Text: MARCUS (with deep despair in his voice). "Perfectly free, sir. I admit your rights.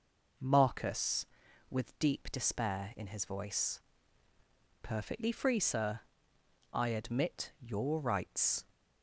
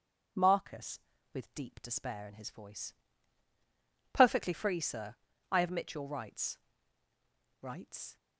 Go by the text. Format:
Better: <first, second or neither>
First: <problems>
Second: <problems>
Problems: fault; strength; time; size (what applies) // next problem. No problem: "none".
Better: first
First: none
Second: says "rights" twice; at 7.6 s